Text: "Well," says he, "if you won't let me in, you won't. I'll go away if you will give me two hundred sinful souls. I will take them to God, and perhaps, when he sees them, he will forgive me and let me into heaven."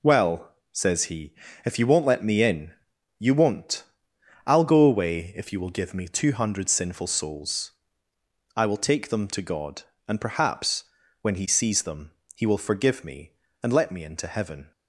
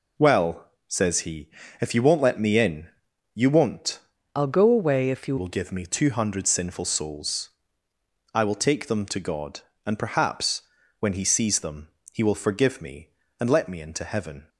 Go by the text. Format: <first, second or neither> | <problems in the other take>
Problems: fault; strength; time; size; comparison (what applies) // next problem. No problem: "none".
first | changes voice from "I'll" to "you"; from 4.3 to 5.3 s; 1.0 s long